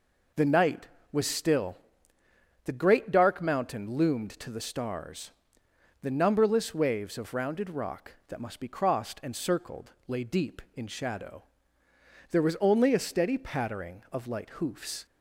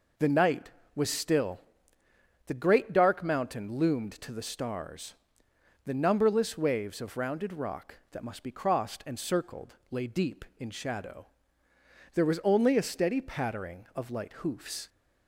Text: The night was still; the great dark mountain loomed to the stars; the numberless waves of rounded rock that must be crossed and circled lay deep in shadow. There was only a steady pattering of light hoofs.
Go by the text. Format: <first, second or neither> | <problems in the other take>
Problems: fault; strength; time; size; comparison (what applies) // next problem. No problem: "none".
neither | pauses between "circled" and "lay"; slight; the same in both